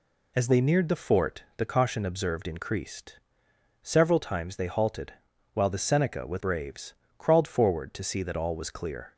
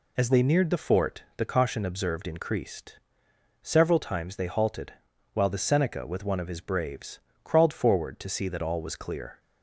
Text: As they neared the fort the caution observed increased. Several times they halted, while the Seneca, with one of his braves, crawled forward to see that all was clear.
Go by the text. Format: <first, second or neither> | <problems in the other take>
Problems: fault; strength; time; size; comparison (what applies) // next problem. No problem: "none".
second | skips "one of his"; at 6.3 s